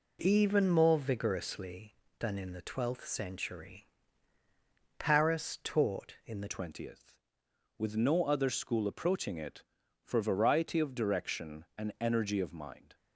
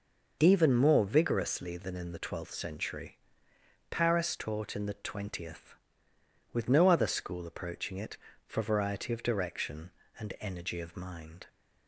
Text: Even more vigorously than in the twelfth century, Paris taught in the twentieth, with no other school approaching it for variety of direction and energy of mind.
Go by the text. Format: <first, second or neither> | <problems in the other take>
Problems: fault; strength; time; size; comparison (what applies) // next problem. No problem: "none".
second | changes voice at "twentieth"; from 6.4 s on; 6.5 s long